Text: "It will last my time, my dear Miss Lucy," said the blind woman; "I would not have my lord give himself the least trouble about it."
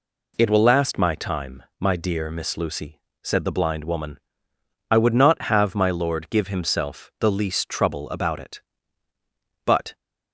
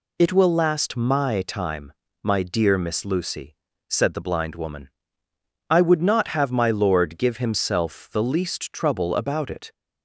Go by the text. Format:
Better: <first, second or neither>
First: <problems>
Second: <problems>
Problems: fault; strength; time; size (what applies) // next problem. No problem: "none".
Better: second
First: goes on to say "But"; slight; from 9.6 s on; 0.30 s long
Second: none